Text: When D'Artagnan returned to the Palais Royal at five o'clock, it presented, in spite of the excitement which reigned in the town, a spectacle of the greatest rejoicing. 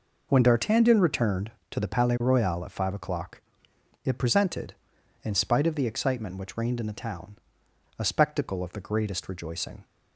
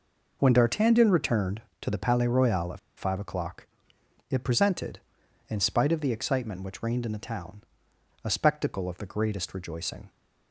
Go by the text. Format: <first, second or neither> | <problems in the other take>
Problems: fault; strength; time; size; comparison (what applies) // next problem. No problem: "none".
first | pauses between "at" and "five"; slight; at 2.7 s; 0.18 s long